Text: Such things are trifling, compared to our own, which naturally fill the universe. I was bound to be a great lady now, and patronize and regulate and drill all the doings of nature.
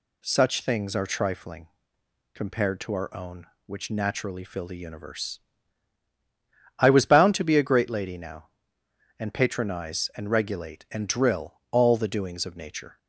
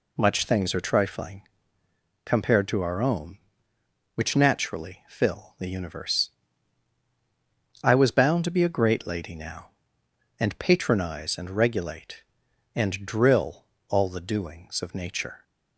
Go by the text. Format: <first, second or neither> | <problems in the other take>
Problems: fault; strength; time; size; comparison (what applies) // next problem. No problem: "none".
first | says "Much" for "Such"; at 0.1 s // pauses between "drill" and "all"; slight; at 13.6 s; 0.24 s long; slight in the first